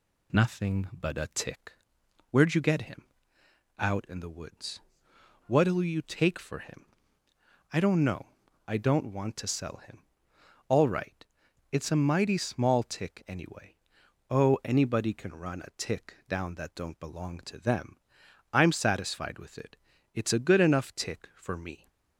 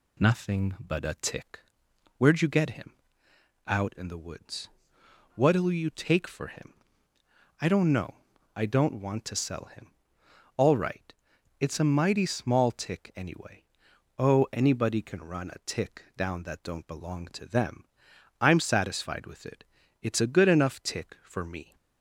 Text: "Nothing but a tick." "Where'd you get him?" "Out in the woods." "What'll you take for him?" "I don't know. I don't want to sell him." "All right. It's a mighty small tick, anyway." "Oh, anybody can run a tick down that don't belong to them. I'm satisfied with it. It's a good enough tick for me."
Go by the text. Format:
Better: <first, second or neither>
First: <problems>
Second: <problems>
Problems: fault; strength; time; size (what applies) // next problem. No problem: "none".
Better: neither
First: none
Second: none